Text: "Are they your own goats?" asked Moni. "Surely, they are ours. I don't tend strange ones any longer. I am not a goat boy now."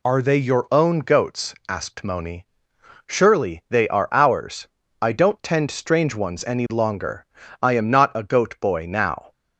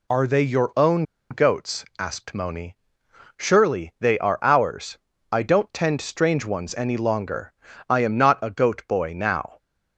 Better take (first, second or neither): first